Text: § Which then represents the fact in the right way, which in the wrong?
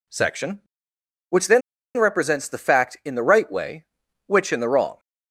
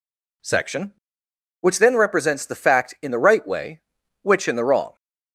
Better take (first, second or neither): second